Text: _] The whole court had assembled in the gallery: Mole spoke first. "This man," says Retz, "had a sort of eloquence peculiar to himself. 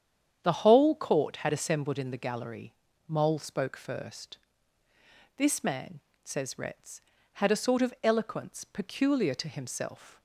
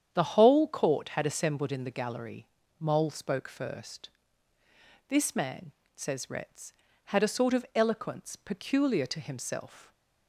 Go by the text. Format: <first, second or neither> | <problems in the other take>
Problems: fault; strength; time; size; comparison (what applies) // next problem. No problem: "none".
neither | starts louder than the rest; strong; the same in both